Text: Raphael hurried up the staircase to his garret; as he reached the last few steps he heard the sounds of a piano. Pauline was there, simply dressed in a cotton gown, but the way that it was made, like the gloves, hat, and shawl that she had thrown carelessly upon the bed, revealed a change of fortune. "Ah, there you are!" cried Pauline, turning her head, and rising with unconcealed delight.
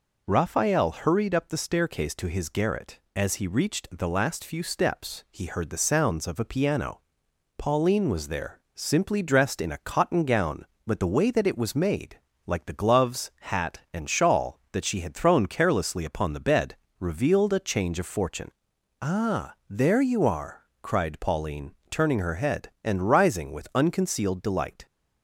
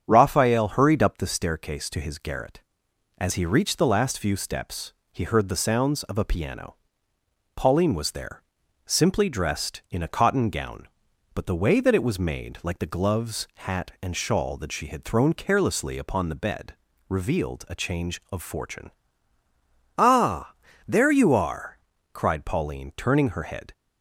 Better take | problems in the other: first | starts louder than the rest; strong; until 1.1 s; 7.5 dB // pauses between "steps" and "he"; slight; at 4.9 s; 0.20 s long // stops before "and rising with unconcealed delight"; at 23.7 s

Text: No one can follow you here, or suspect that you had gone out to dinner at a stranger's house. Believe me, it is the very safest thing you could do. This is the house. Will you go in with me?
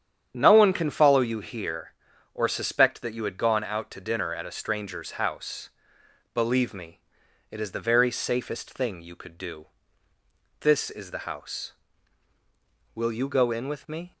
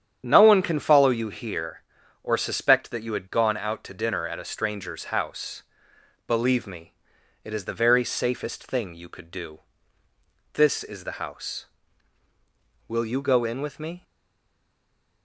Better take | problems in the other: first | starts louder than the rest; strong; until 1.2 s; 9 dB; strong in the first // stays silent after the last word; noticeable; from 14.0 s on; 1.2 s long

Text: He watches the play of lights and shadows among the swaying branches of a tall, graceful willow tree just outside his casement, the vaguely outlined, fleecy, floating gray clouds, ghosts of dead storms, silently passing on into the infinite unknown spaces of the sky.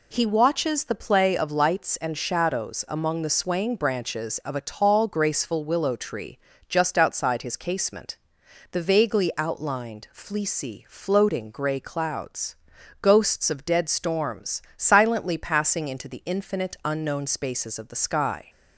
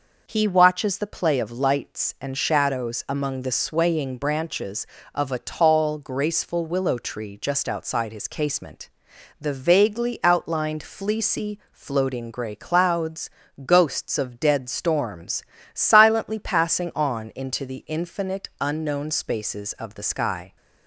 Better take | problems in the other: second | pauses between "tree" and "just"; slight; at 6.3 s; 0.30 s long // skips "on"; at 15.8 s

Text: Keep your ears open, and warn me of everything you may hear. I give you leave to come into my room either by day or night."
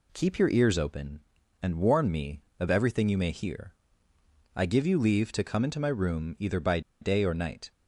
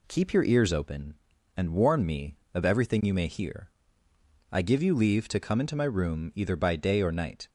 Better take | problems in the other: second | pauses between "by" and "day"; slight; at 6.8 s; 0.20 s long

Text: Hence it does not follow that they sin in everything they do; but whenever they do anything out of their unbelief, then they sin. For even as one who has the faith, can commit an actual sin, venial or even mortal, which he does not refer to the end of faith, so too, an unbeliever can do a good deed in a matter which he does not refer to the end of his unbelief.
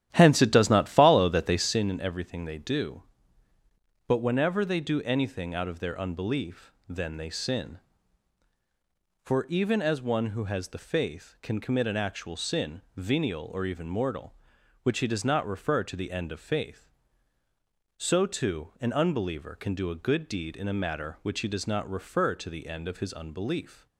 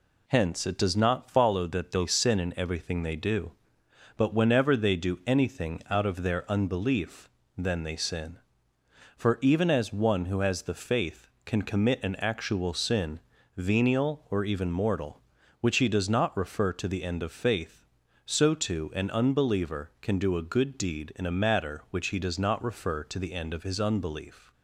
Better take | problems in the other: second | starts louder than the rest; strong; until 1.9 s; 11.5 dB

